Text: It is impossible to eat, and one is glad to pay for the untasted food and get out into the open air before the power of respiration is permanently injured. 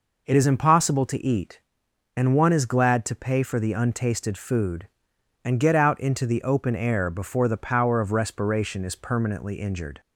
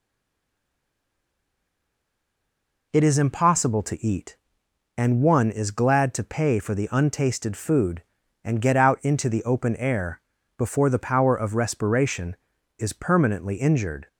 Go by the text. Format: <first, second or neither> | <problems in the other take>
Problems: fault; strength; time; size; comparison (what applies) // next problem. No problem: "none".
first | stays silent before the first word; strong; until 2.9 s; 2.9 s long // pauses between "air" and "before"; slight; at 10.2 s; 0.36 s long